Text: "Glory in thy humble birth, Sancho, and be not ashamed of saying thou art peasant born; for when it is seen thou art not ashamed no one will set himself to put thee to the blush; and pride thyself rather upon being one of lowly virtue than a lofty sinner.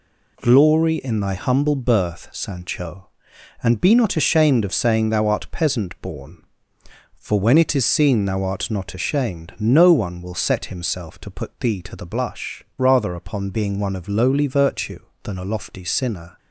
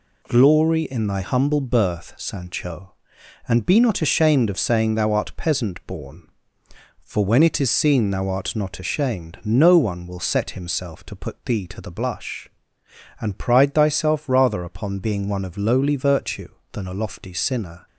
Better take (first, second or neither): second